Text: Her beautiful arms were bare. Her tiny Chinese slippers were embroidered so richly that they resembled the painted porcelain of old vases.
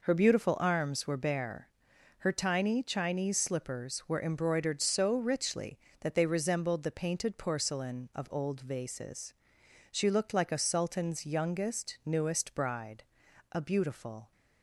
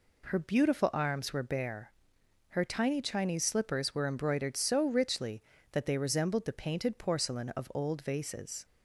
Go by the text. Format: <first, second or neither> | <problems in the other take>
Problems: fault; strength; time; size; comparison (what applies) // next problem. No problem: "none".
second | goes on to say "She looked like a sultan's youngest newest bride a beautiful"; strong; from 9.9 s on; 4.4 s long